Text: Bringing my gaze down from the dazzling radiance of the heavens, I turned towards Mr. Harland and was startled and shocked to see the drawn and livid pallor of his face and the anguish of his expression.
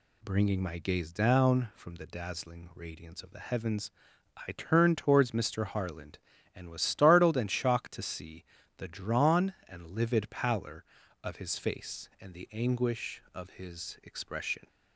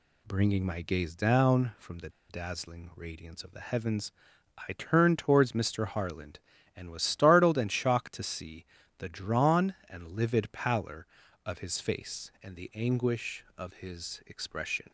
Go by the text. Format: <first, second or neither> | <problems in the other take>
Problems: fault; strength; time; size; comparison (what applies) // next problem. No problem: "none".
first | pauses between "the" and "dazzling"; slight; at 2.0 s; 0.20 s long // pauses between "see" and "the"; slight; at 8.6 s; 0.34 s long; slight in the first